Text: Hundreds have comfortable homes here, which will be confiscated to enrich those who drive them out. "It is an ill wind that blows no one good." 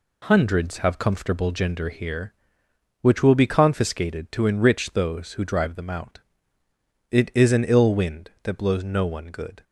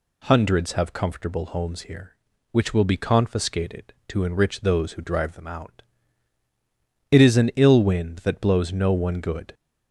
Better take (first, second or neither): second